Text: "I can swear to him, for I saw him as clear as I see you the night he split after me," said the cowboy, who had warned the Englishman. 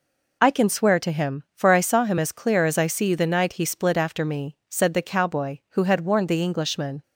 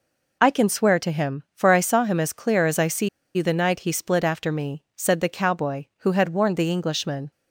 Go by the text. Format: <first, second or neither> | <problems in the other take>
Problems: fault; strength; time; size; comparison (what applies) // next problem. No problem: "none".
first | pauses between "see" and "you"; slight; at 3.0 s; 0.27 s long